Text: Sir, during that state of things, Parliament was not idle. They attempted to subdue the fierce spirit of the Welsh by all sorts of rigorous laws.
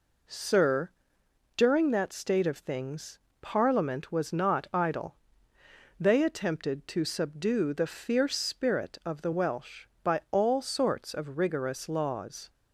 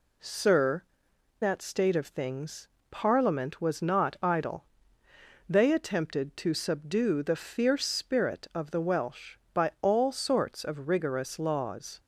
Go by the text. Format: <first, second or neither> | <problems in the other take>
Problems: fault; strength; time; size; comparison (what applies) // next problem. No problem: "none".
first | skips "during"; at 1.1 s